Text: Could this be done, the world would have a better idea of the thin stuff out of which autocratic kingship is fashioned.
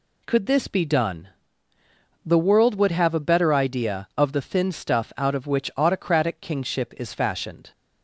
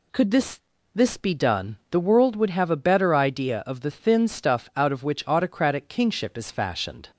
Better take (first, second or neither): first